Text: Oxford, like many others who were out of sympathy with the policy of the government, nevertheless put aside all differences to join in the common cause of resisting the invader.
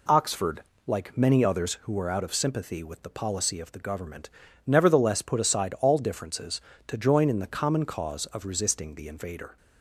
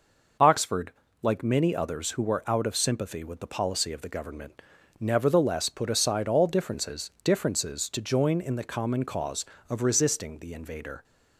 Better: first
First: none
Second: says "differences" twice; at 7.2 s

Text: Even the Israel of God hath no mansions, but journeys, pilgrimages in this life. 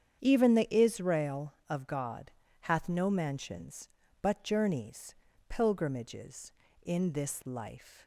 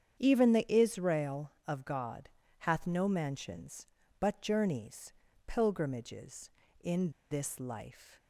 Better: first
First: starts louder than the rest; strong; until 1.2 s; 8 dB // pauses between "God" and "hath"; slight; at 2.3 s; 0.30 s long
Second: starts louder than the rest; strong; until 1.2 s; 8 dB // pauses between "God" and "hath"; slight; at 2.2 s; 0.30 s long // pauses between "in" and "this"; slight; at 7.0 s; 0.21 s long

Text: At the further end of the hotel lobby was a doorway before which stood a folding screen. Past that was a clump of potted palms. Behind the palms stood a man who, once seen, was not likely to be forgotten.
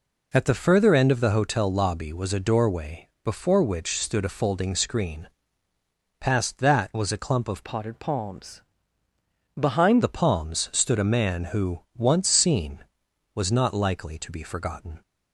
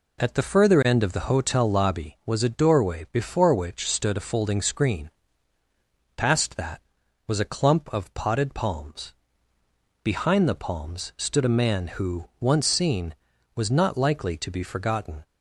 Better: second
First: pauses between "doorway" and "before"; slight; at 3.0 s; 0.16 s long // changes voice from "potted" to "Behind"; from 7.6 to 10.0 s; 2.4 s long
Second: none

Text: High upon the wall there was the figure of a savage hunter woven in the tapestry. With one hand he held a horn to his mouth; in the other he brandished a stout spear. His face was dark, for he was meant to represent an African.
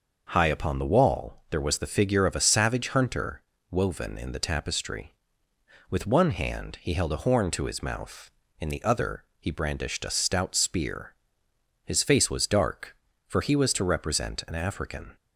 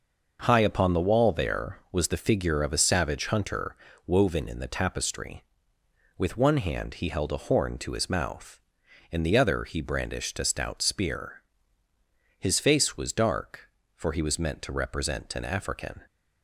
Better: second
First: pauses between "hunter" and "woven"; slight; at 3.3 s; 0.30 s long // pauses between "other" and "he"; slight; at 9.2 s; 0.16 s long // skips "meant"; at 13.7 s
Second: pauses between "hunter" and "woven"; slight; at 3.7 s; 0.32 s long

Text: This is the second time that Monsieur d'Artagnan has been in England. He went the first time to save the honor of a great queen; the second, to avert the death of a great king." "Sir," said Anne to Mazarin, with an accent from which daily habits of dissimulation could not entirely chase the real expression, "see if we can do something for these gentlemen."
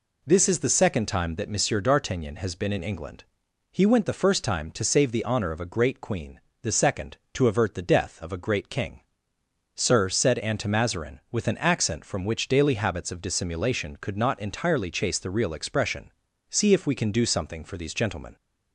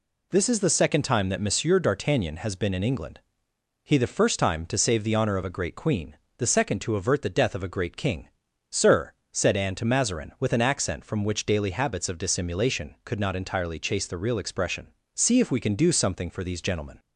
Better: first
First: none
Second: skips "went"; at 3.9 s

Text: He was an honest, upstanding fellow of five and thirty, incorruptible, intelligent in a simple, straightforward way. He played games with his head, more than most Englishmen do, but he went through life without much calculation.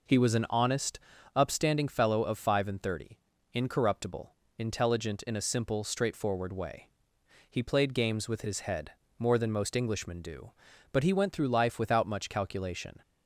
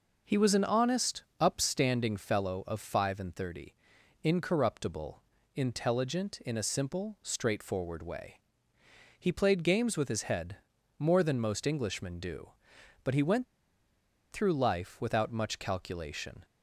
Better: first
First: none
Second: pauses between "went" and "through"; noticeable; at 13.4 s; 0.87 s long

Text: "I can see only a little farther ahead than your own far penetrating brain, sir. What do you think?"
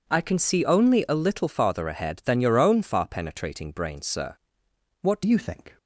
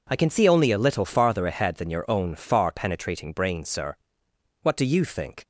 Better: second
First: changes voice at "you"; from 5.2 s on; 0.5 s long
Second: none

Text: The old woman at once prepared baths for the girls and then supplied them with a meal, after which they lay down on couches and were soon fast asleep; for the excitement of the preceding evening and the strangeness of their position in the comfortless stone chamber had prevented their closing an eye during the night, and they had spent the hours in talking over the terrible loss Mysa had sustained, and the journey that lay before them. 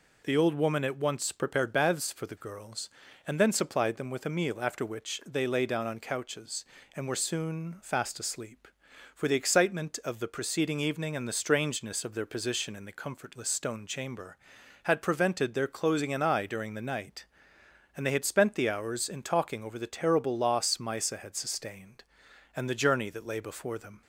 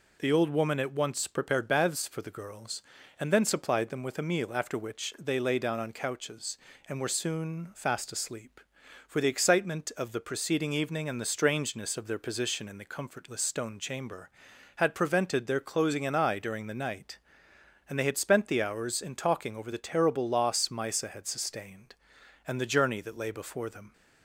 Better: neither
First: none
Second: none

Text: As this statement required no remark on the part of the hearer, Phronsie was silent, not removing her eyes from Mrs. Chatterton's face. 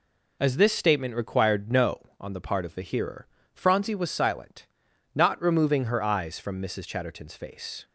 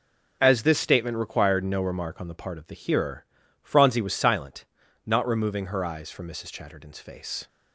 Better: second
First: skips "remark"; at 2.1 s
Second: none

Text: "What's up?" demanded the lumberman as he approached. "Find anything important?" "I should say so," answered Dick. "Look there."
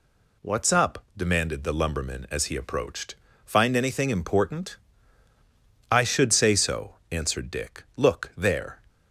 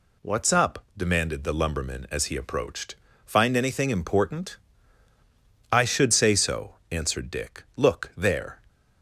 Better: neither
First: none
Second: none

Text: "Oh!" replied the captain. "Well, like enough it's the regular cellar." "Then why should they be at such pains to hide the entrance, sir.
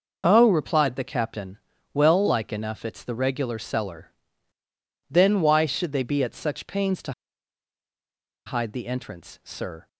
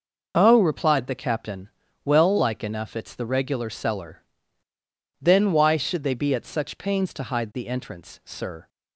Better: second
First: pauses between "to" and "hide"; strong; at 7.1 s; 1.3 s long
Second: none

